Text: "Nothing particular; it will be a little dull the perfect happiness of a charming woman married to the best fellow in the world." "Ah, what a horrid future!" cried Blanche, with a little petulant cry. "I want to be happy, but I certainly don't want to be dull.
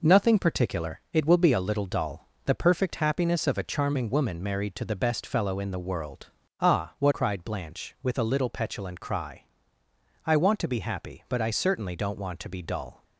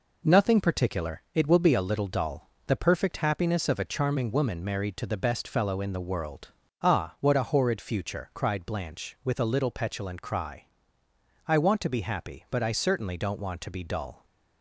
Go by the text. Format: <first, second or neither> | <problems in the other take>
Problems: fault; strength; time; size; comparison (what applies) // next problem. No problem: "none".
second | pauses between "dull" and "the"; slight; at 2.2 s; 0.18 s long; slight in the second // skips "a horrid future"; at 7.1 s